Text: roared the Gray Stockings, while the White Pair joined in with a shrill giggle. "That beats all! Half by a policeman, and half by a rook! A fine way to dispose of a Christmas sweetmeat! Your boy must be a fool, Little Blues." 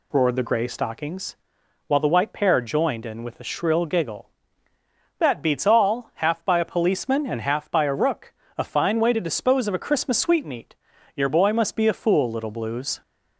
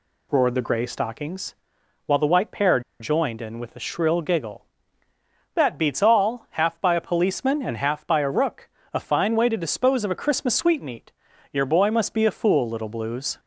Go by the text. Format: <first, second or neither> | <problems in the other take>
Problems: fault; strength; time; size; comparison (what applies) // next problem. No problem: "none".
first | pauses between "Pair" and "joined"; slight; at 2.8 s; 0.20 s long